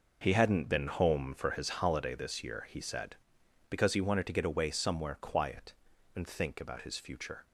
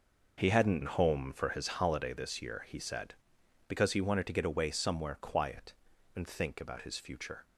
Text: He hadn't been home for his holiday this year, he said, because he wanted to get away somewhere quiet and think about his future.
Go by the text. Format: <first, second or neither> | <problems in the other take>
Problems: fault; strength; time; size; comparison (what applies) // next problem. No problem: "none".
first | skips "been"; at 0.8 s